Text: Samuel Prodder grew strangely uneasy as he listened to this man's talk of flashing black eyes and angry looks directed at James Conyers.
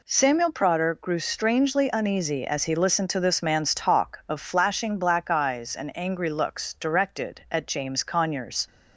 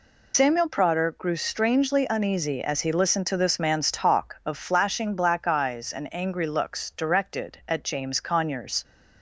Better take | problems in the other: first | loses the start of "Samuel"; at 0.3 s; 135 ms

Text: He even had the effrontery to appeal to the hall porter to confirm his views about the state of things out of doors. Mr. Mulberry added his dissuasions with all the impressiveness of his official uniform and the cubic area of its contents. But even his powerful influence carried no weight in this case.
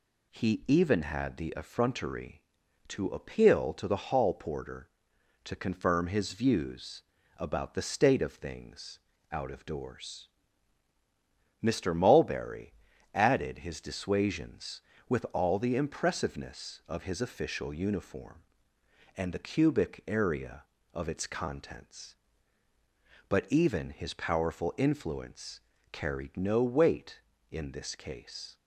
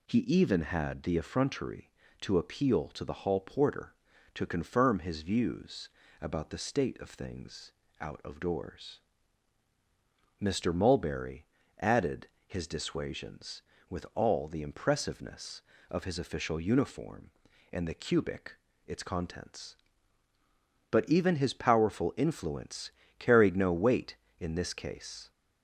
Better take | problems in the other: first | pauses between "views" and "about"; slight; at 5.8 s; 0.32 s long; slight in the first // pauses between "things" and "out"; slight; at 7.7 s; 0.26 s long; slight in the first // pauses between "Mulberry" and "added"; slight; at 11.4 s; 0.36 s long; also in the first // pauses between "added" and "his"; slight; at 12.2 s; 0.18 s long // skips "area of"; at 18.7 s // pauses between "influence" and "carried"; slight; at 22.9 s; 0.28 s long; slight in the first

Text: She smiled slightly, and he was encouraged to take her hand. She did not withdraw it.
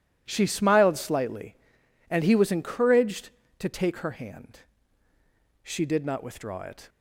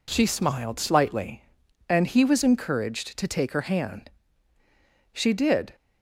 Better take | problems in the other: first | stops before "not withdraw it"; at 5.7 s

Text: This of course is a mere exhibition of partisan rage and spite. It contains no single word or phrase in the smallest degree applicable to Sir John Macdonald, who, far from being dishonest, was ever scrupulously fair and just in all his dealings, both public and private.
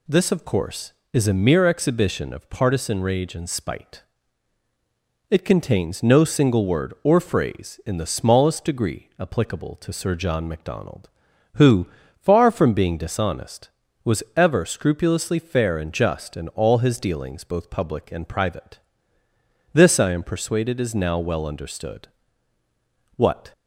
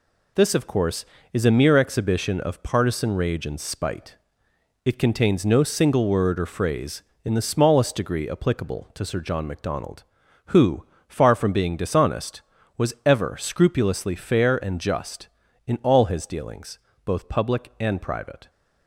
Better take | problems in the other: second | goes on to say "This I am persuaded is now well understood What"; strong; from 19.7 s on; 3.7 s long

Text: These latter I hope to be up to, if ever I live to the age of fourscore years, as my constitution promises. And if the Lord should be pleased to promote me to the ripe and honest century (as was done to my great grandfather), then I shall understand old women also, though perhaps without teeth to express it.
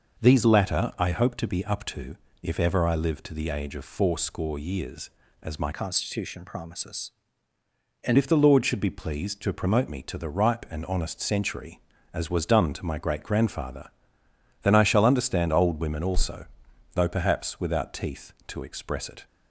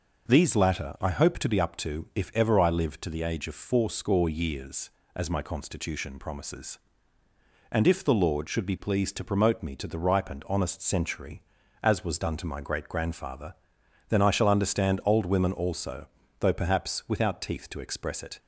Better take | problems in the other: second | changes voice from "constitution" to "And"; from 5.7 to 8.1 s; 2.4 s long

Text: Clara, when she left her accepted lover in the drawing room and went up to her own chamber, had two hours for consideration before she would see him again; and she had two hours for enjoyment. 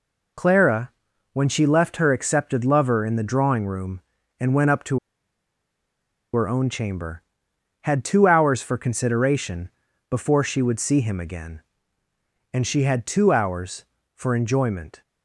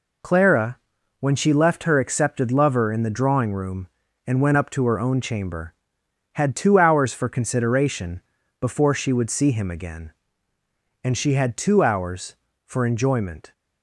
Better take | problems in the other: second | pauses between "to" and "her"; strong; at 4.9 s; 1.3 s long // pauses between "consideration" and "before"; at 9.6 s; 0.40 s long; also in the second

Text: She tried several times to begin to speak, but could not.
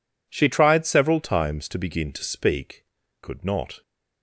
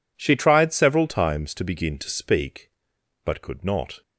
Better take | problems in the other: second | skips "but"; at 3.0 s

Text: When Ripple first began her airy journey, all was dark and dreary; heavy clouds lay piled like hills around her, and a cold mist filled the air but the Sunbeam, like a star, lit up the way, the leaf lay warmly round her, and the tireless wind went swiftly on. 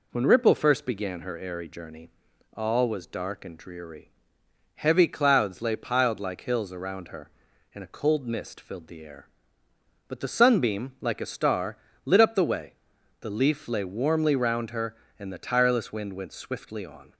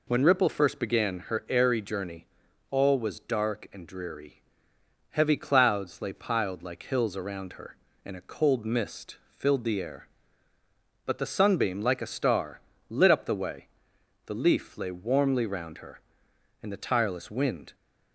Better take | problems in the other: first | stops before "went swiftly on"; at 17.7 s

